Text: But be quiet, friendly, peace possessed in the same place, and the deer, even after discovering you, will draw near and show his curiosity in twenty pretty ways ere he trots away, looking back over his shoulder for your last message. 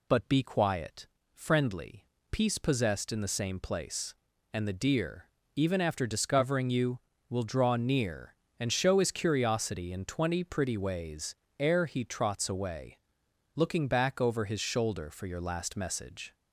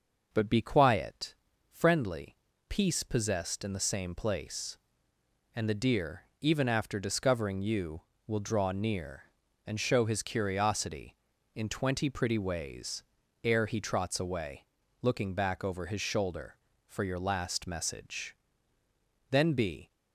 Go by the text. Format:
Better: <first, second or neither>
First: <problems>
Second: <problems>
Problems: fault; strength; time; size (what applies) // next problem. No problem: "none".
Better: first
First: pauses between "ways" and "ere"; slight; at 11.3 s; 0.22 s long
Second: pauses between "ways" and "ere"; at 13.0 s; 0.40 s long // goes on to say "Then be"; from 19.3 s on; 0.60 s long